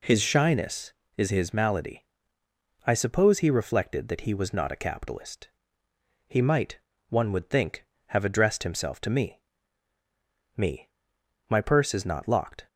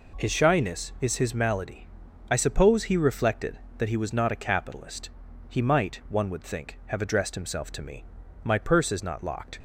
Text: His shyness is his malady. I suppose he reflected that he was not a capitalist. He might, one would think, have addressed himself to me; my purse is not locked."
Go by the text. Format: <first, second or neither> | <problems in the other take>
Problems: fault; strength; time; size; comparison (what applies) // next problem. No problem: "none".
second | says "me" twice; at 10.5 s